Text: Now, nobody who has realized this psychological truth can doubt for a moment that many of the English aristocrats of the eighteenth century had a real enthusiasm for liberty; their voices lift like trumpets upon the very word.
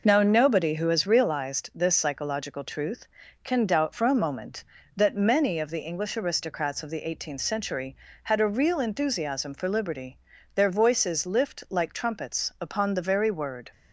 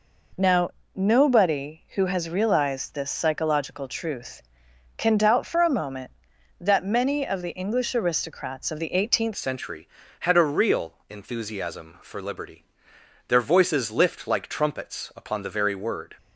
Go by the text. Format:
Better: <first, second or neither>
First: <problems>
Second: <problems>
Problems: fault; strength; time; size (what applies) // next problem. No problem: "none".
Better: first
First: none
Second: changes voice at "century"; from 9.3 s on; 6.8 s long // pauses between "real" and "enthusiasm"; slight; at 10.9 s; 0.16 s long